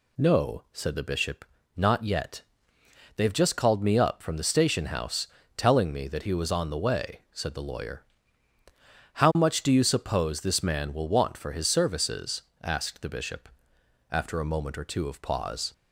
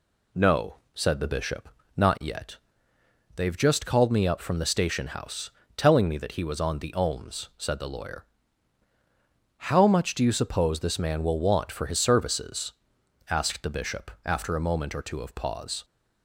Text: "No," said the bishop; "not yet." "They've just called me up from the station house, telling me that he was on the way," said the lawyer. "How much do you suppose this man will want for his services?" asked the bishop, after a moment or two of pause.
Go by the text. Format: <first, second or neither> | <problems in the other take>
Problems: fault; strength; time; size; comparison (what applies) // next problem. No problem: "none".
first | says "ohms" for "way"; at 6.9 s